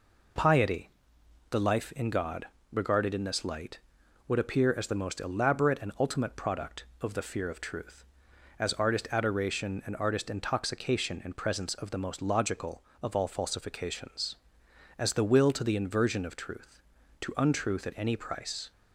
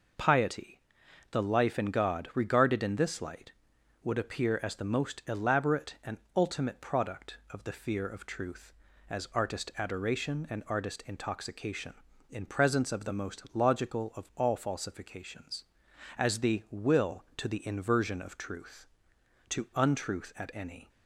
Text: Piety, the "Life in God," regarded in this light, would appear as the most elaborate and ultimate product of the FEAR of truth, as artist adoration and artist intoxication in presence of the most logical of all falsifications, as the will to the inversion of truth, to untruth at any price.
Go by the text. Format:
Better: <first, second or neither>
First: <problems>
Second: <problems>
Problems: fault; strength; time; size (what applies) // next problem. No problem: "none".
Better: first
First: none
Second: pauses between "and" and "ultimate"; slight; at 6.1 s; 0.18 s long // stops before "price"; at 20.8 s